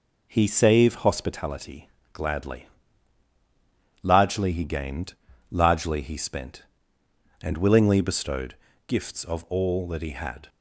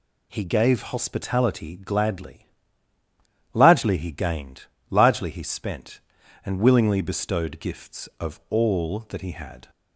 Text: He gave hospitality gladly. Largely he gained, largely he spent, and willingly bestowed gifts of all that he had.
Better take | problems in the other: second | says "save" for "gave"; at 0.4 s // pauses between "hospitality" and "gladly"; slight; at 1.8 s; 0.24 s long // pauses between "bestowed" and "gifts"; slight; at 8.5 s; 0.34 s long

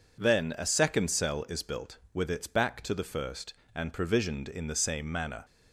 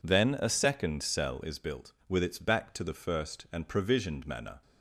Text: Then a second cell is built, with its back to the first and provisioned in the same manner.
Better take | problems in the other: first | skips "in the same"; at 4.2 s

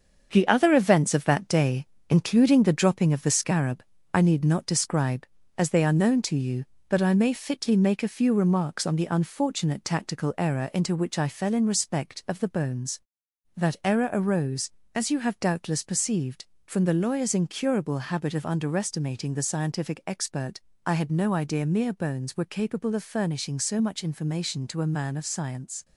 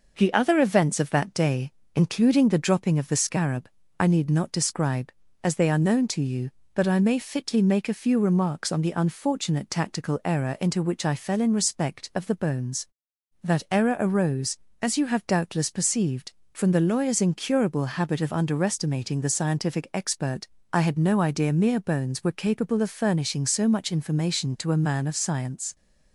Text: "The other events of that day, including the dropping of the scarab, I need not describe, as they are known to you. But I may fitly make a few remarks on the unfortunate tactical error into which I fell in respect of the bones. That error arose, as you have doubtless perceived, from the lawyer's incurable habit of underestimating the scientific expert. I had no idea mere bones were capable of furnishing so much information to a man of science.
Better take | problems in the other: second | gets quieter; noticeable; throughout; 6 dB

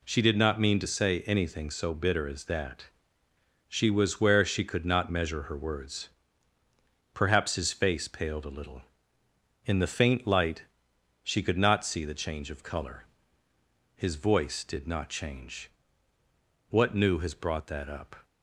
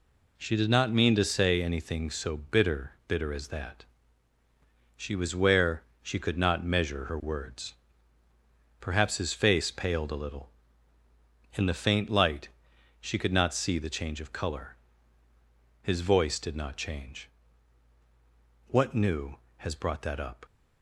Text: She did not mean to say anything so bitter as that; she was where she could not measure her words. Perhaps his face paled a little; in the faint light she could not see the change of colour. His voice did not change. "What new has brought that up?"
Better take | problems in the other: first | says "bitter" twice; at 3.0 s // pauses between "where" and "she"; slight; at 5.8 s; 0.18 s long // pauses between "light" and "she"; noticeable; at 12.4 s; 0.52 s long; noticeable in the first

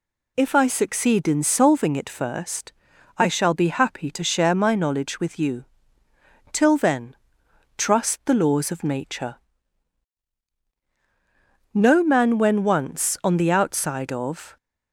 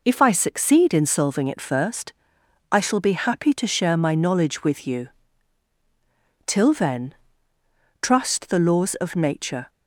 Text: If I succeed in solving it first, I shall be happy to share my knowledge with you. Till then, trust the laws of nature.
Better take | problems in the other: second | goes on to say "No man when once on the outside of"; strong; from 11.7 s on; 2.8 s long

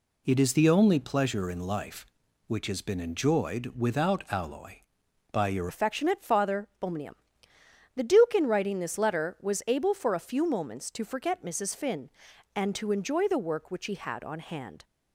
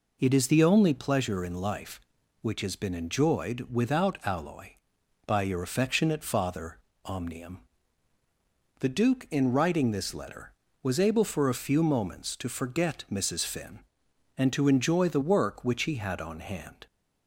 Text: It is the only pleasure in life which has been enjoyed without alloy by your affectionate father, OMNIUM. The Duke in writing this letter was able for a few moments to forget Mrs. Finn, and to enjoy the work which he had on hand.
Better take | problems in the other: second | changes voice at "affectionate"; from 5.6 s on; 9.2 s long

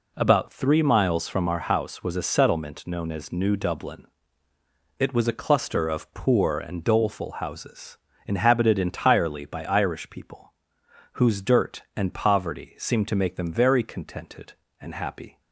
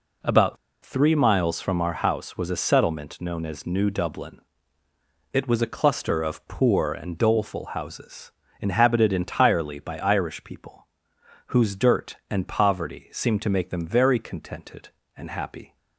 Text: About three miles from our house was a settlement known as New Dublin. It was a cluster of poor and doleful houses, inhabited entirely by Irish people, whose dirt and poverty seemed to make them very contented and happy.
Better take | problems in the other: first | pauses between "About" and "three"; slight; at 0.5 s; 0.27 s long

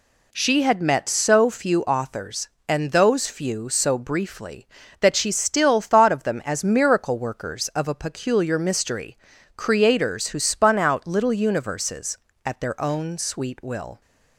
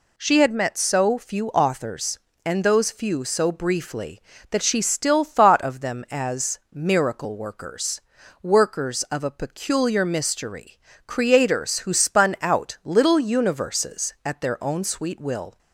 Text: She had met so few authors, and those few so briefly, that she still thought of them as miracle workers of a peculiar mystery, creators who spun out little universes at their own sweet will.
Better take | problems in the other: first | says "workers" twice; at 8.4 s

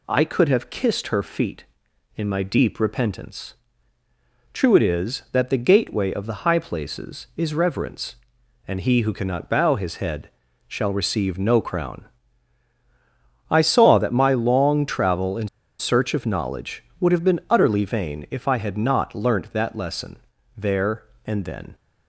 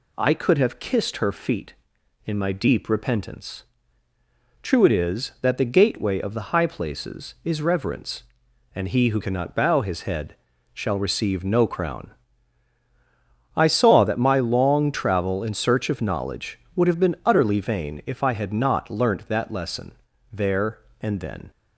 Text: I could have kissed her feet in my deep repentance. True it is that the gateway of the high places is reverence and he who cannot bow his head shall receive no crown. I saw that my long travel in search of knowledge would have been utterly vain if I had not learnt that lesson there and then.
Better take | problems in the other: second | pauses between "head" and "shall"; slight; at 10.3 s; 0.36 s long; slight in the second // pauses between "in" and "search"; slight; at 15.4 s; 0.30 s long // pauses between "lesson" and "there"; at 20.1 s; 0.40 s long; also in the second

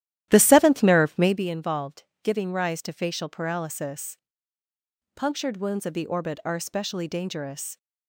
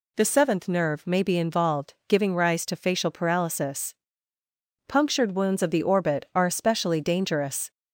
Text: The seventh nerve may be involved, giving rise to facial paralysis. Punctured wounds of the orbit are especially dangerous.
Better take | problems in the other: second | starts louder than the rest; strong; until 1.4 s; 13 dB

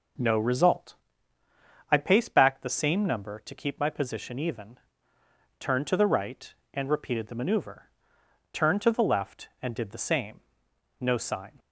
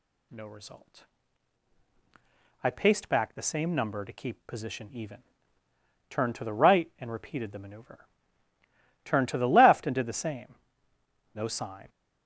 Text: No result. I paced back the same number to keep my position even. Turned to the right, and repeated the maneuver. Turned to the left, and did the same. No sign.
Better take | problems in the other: first | skips "my"; at 4.4 s

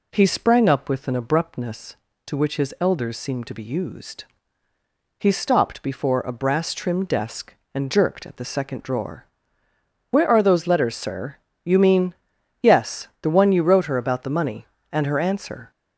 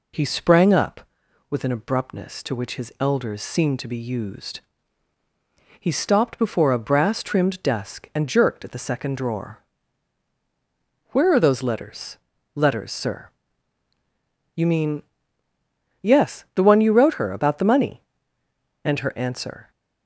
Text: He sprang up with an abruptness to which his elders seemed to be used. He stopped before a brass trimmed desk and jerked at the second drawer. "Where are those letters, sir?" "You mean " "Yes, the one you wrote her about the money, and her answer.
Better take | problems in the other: first | says "letters" twice; at 12.5 s

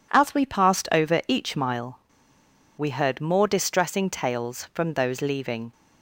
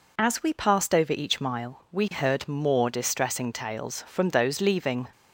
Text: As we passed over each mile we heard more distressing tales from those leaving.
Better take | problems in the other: second | pauses between "mile" and "we"; noticeable; at 1.9 s; 0.78 s long

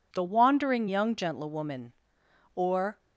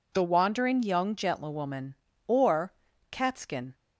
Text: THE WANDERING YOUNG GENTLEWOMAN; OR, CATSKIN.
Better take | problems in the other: second | stops before "CATSKIN"; at 2.9 s

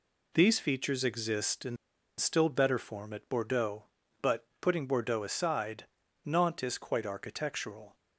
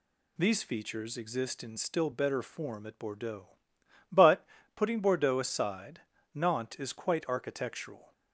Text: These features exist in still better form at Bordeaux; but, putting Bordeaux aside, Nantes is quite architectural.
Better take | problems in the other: second | pauses between "in" and "still"; at 1.7 s; 0.41 s long

